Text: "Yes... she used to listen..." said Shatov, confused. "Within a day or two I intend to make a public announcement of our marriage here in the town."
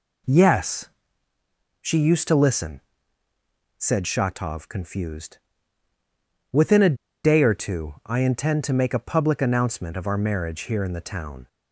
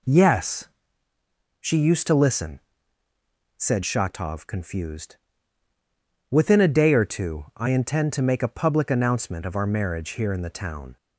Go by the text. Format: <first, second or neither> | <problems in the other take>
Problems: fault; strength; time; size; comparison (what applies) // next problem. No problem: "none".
second | pauses between "a" and "day"; slight; at 6.9 s; 0.28 s long